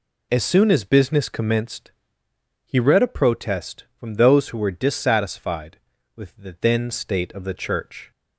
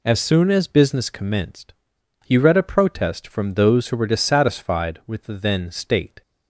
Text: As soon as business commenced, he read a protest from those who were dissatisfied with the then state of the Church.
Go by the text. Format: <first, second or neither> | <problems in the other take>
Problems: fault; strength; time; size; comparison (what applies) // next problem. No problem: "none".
first | stops before "of the Church"; at 6.2 s